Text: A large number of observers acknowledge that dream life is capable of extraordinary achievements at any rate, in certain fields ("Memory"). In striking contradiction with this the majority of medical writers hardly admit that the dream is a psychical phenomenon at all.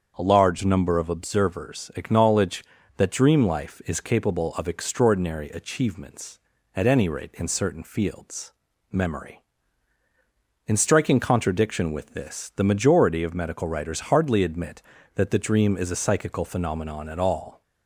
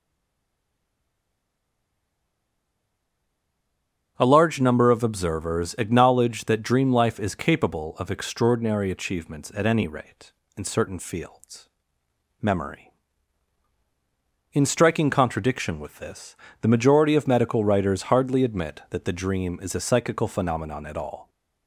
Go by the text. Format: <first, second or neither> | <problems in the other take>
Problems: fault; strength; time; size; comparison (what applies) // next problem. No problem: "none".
first | stays silent before the first word; strong; until 4.1 s; 4.1 s long // starts louder than the rest; strong; until 5.1 s; 8.5 dB; strong in the first // pauses between "this" and "the"; slight; at 16.3 s; 0.24 s long